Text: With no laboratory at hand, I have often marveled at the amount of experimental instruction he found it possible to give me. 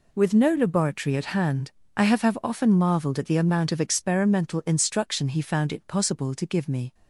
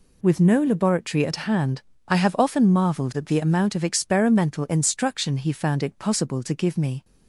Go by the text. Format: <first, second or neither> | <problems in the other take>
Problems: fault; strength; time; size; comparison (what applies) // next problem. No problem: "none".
second | says "have" twice; at 2.2 s